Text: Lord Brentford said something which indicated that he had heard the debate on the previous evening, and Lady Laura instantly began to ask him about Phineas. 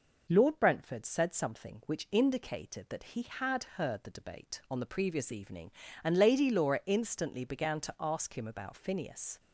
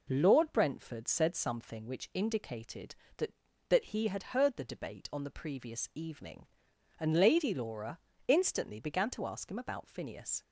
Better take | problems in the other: first | says "that" twice; at 3.6 s // pauses between "Laura" and "instantly"; slight; at 7.9 s; 0.28 s long

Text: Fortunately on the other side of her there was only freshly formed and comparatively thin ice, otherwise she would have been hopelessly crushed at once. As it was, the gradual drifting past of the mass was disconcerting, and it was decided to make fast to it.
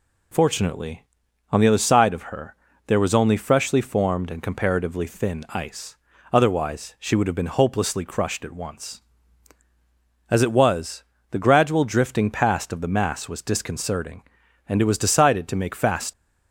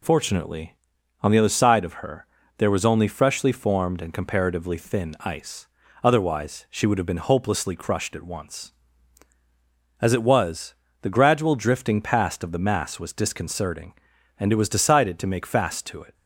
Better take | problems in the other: second | pauses between "her" and "there"; slight; at 2.5 s; 0.30 s long; slight in the second // stops before "to it"; at 16.1 s

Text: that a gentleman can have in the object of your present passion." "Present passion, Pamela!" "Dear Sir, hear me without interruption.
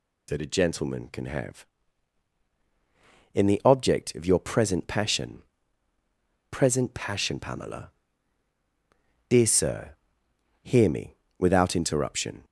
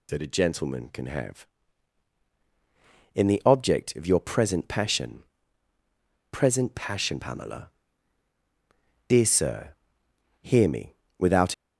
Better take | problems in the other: first | pauses between "me" and "without"; slight; at 10.9 s; 0.22 s long; slight in the first // stops before "interruption"; at 11.5 s

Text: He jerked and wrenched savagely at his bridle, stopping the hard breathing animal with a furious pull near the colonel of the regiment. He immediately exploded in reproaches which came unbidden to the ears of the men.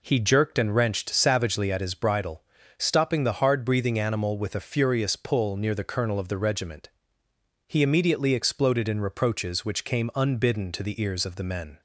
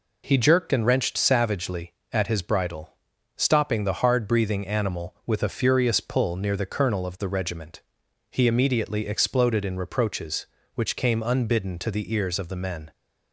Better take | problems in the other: neither | none

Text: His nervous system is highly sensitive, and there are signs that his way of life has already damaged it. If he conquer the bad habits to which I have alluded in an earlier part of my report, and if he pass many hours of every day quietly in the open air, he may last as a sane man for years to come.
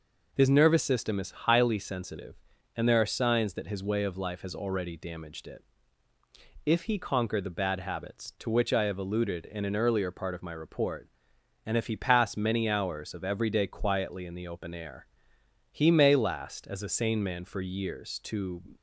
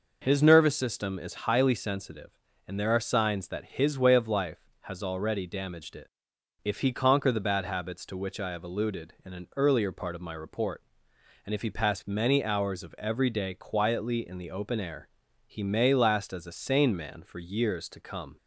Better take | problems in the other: second | stops before "come"; at 18.7 s

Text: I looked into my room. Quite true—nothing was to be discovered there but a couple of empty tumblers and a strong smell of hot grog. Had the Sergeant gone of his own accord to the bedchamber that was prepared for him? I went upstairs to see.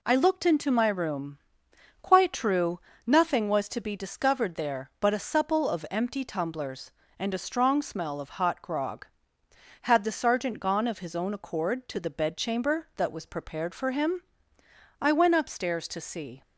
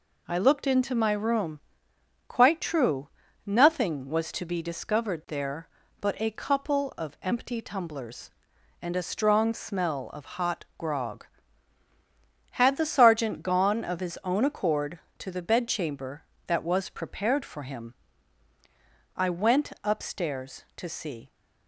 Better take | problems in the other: second | says "supple" for "couple"; at 5.1 s

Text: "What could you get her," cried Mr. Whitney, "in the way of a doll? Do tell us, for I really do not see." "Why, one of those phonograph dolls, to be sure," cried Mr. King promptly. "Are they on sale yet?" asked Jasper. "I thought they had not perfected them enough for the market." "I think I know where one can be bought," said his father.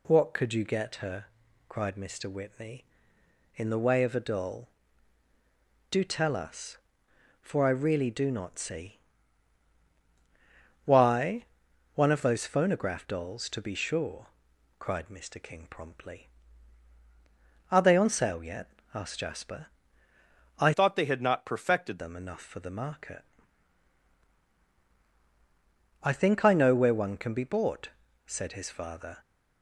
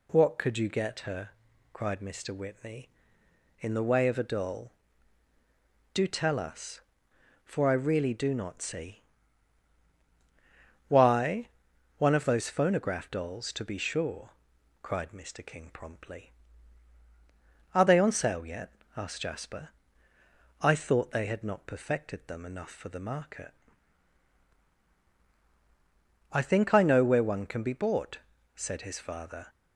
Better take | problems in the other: second | changes voice from "thought" to "perfected"; from 20.7 to 21.9 s; 1.2 s long

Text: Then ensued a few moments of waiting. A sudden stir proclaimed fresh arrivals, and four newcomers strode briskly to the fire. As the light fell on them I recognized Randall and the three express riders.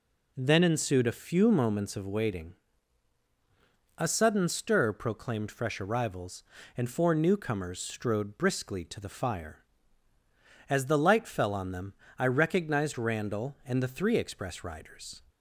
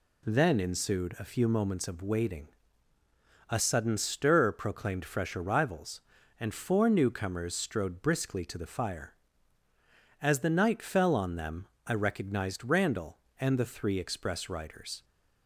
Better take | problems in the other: first | says "night" for "light"; at 10.5 s // pauses between "them" and "I"; slight; at 11.6 s; 0.20 s long; slight in the first

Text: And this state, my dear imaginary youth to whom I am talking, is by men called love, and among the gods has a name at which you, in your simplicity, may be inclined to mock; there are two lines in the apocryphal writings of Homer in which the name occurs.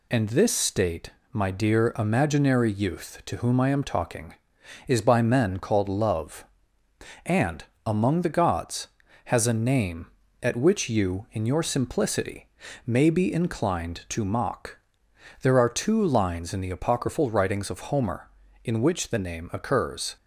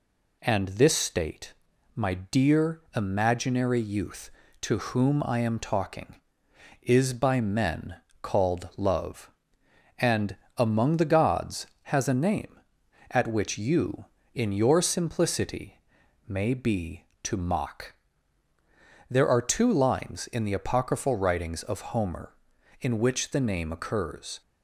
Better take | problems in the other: first | pauses between "men" and "called"; slight; at 7.9 s; 0.26 s long // pauses between "and" and "among"; slight; at 10.3 s; 0.22 s long; slight in the first // skips "inclined"; at 17.1 s

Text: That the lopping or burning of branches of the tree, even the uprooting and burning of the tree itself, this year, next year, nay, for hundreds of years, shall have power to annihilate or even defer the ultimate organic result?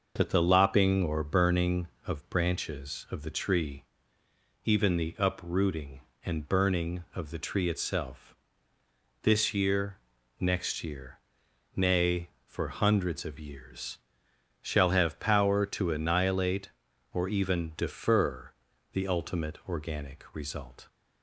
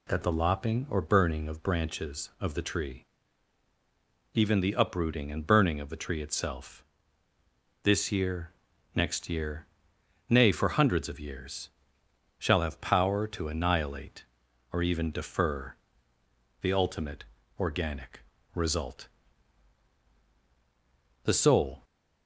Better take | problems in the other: first | pauses between "defer" and "the"; noticeable; at 15.7 s; 0.88 s long; also in the first // pauses between "ultimate" and "organic"; slight; at 17.2 s; 0.36 s long // pauses between "organic" and "result"; slight; at 18.2 s; 0.32 s long // goes on to say "The soul"; from 21.2 s on; 0.60 s long

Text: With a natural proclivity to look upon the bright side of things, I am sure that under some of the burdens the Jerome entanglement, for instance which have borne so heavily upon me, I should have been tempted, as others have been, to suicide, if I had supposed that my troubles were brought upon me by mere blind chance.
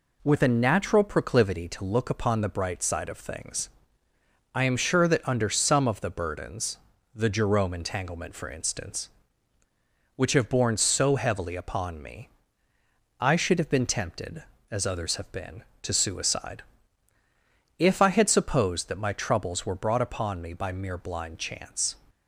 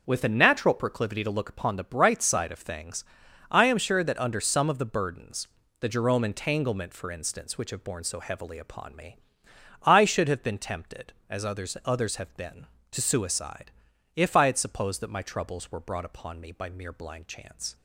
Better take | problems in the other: first | pauses between "burdens" and "the"; slight; at 5.4 s; 0.34 s long; also in the first // says "others" twice; at 11.8 s

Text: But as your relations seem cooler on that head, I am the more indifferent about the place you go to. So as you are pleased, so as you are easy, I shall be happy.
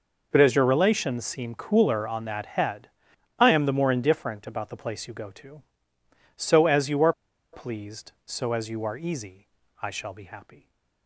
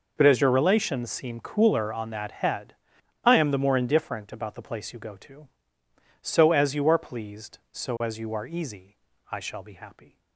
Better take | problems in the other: second | pauses between "are" and "pleased"; at 7.1 s; 0.40 s long

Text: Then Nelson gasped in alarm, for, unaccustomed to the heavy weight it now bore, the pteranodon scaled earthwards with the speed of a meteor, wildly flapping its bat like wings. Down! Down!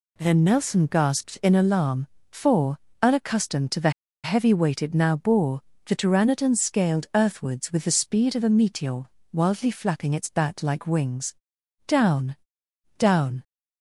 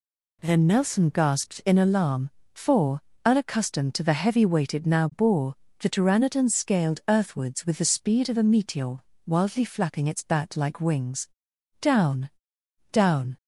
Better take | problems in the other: second | pauses between "the" and "heavy"; slight; at 3.8 s; 0.34 s long

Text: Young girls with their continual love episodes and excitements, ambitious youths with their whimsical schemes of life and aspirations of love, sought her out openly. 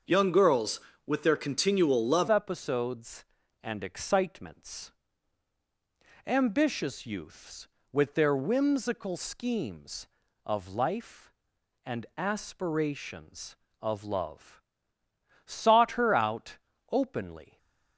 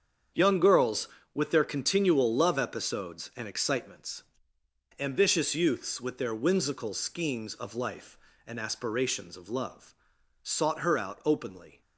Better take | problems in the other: second | starts louder than the rest; until 1.3 s; 6.5 dB; strong in the second // changes voice at "episodes"; from 2.2 s on; 15.3 s long // pauses between "out" and "openly"; slight; at 16.5 s; 0.32 s long

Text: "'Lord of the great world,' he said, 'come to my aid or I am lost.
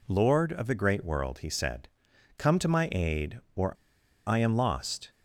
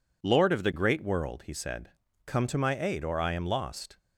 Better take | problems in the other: second | pauses between "or" and "I"; noticeable; at 3.7 s; 0.54 s long

